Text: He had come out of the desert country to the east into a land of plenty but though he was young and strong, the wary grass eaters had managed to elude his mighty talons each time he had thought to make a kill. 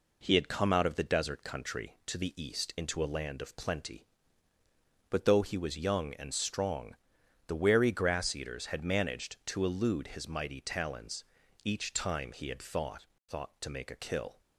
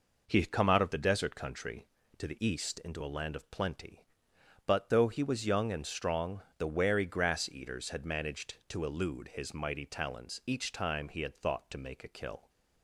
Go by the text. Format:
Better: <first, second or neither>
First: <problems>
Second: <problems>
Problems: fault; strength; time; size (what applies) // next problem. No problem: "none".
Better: second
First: pauses between "talons" and "each"; at 11.2 s; 0.40 s long // says "thought" twice; at 13.2 s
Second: none